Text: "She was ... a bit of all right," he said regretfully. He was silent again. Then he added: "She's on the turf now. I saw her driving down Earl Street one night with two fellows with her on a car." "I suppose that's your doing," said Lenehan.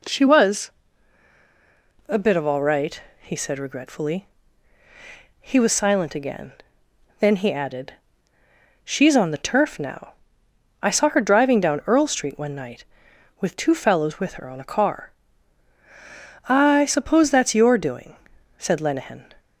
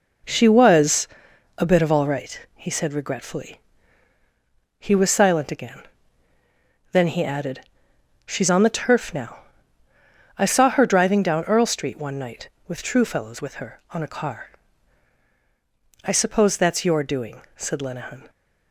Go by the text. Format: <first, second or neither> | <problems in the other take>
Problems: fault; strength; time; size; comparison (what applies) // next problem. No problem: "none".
first | says "true" for "two"; at 12.8 s